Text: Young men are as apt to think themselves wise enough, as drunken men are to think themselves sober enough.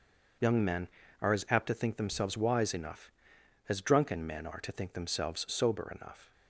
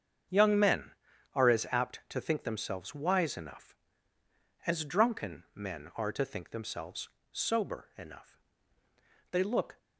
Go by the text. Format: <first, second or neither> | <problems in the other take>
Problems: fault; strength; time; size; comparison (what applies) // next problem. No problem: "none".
first | starts louder than the rest; strong; until 1.7 s; 7.5 dB // pauses between "themselves" and "sober"; slight; at 7.0 s; 0.22 s long // goes on to say "They look"; slight; from 9.3 s on; 0.46 s long